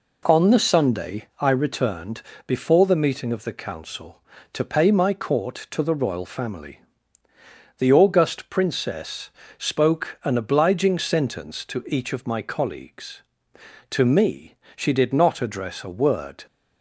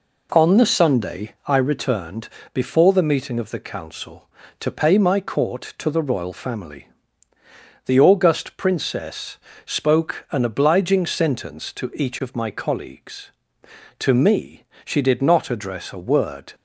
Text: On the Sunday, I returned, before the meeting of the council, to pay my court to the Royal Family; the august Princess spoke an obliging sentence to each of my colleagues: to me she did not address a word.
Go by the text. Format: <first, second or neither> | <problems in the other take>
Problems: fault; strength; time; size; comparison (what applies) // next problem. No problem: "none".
neither | pauses between "Princess" and "spoke"; slight; the same in both // pauses between "me" and "she"; slight; the same in both